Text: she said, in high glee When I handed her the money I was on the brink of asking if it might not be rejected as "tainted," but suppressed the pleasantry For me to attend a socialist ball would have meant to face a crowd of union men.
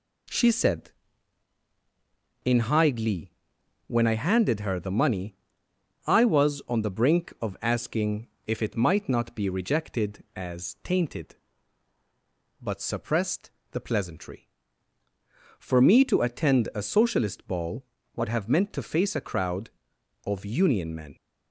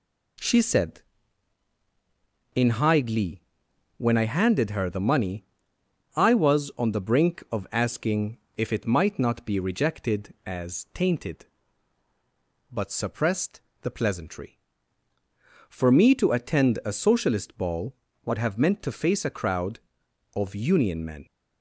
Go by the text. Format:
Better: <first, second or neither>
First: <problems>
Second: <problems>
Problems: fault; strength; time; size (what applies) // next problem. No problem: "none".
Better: neither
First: pauses between "glee" and "When"; noticeable; at 3.3 s; 0.56 s long // pauses between "money" and "I"; noticeable; at 5.3 s; 0.70 s long // pauses between "asking" and "if"; slight; at 8.2 s; 0.18 s long // pauses between "suppressed" and "the"; slight; at 13.4 s; 0.22 s long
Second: pauses between "glee" and "When"; noticeable; at 3.4 s; 0.56 s long // pauses between "money" and "I"; noticeable; at 5.4 s; 0.70 s long // pauses between "asking" and "if"; slight; at 8.3 s; 0.18 s long // pauses between "suppressed" and "the"; slight; at 13.6 s; 0.22 s long